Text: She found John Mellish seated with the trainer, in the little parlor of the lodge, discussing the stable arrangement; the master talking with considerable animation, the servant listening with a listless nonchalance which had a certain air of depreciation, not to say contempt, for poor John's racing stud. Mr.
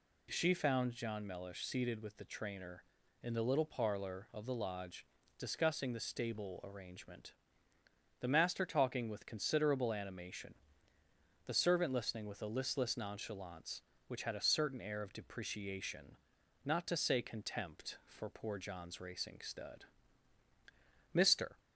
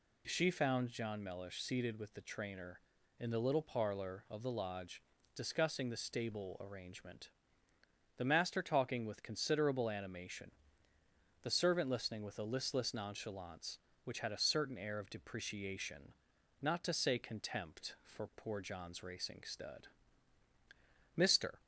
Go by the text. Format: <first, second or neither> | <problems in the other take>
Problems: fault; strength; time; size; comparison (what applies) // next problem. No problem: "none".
neither | none